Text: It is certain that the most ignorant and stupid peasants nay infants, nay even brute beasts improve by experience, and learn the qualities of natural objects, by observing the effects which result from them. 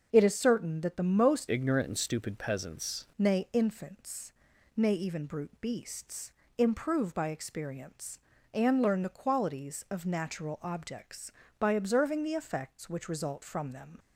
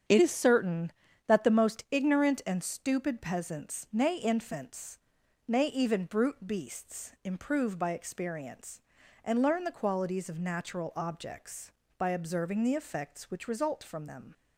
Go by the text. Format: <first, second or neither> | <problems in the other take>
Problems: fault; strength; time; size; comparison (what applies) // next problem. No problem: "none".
second | starts louder than the rest; until 1.1 s; 6.5 dB; strong in the second // changes voice from "ignorant" to "peasants"; from 1.4 to 3.0 s; 1.6 s long // pauses between "beasts" and "improve"; slight; at 6.3 s; 0.24 s long